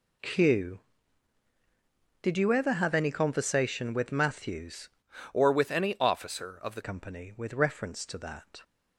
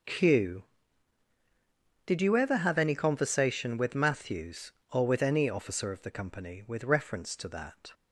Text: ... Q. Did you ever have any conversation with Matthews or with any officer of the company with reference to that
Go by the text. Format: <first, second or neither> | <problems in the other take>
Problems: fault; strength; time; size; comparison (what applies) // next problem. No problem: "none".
second | changes voice from "or" to "the"; from 5.3 to 6.8 s; 1.5 s long